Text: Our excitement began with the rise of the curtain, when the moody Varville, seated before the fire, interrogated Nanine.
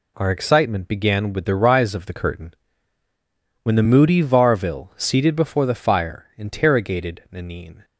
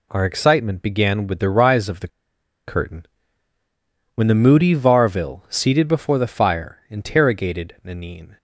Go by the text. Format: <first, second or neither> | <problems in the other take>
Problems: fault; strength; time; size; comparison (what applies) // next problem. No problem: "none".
first | pauses between "the" and "curtain"; noticeable; at 2.0 s; 0.58 s long